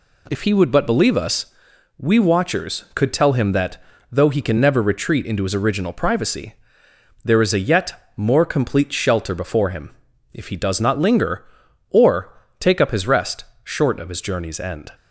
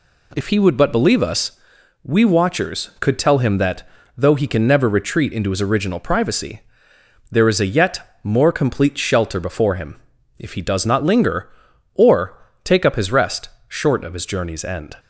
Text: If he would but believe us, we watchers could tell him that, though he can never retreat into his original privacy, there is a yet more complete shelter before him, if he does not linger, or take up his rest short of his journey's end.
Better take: neither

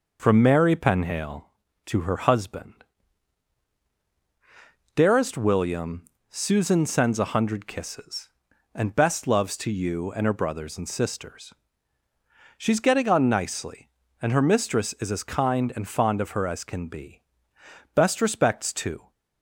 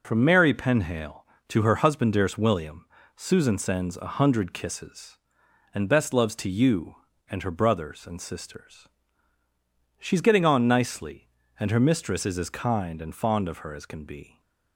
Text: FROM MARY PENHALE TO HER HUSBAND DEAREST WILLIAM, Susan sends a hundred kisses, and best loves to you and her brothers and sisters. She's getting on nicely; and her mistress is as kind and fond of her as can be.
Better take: second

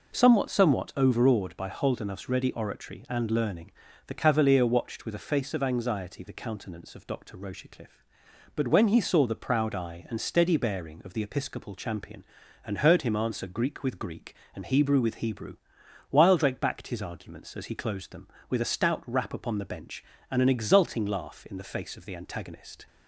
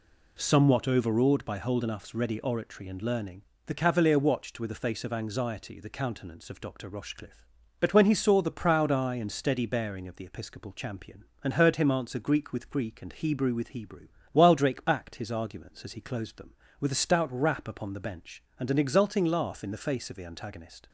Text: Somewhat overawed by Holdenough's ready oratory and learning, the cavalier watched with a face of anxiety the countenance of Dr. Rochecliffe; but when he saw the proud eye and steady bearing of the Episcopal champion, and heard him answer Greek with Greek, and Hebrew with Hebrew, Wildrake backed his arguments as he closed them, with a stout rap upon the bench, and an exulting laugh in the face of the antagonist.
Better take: second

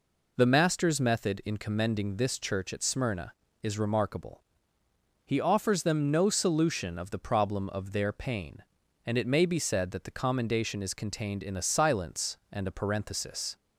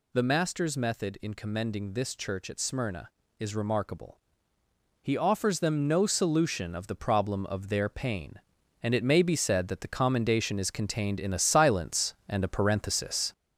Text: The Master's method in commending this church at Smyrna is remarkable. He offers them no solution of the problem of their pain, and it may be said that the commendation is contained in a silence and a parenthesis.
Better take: first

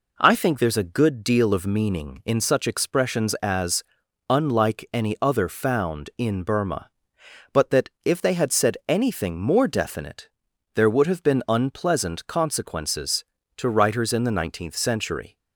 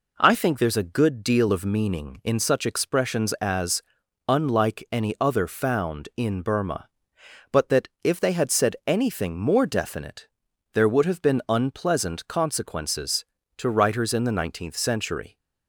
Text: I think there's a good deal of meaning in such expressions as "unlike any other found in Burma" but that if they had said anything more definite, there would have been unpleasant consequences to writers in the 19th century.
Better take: neither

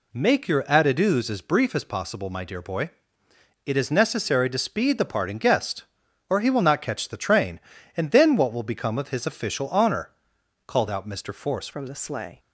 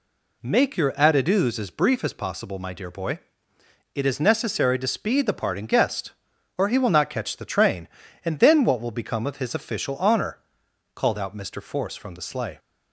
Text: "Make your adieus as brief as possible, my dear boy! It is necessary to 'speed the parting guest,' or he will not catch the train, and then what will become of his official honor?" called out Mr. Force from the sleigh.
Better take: second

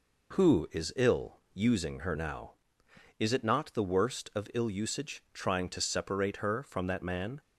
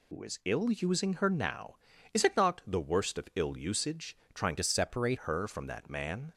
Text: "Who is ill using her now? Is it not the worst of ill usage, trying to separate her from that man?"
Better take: first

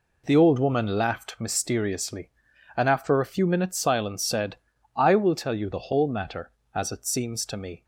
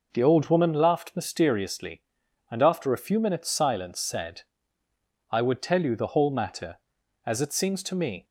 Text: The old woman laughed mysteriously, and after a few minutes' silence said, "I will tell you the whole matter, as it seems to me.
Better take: first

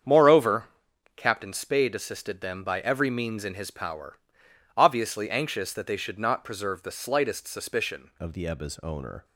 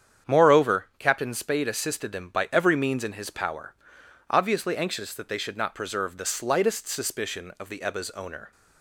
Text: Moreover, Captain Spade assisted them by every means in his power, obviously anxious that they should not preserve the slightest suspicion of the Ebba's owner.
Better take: second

